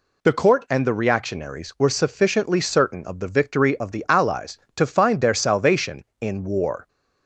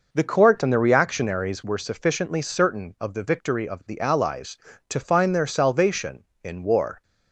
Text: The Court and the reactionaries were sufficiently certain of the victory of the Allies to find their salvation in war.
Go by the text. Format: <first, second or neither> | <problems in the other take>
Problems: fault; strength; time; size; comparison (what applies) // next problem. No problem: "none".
first | starts louder than the rest; noticeable; until 1.8 s; 5.5 dB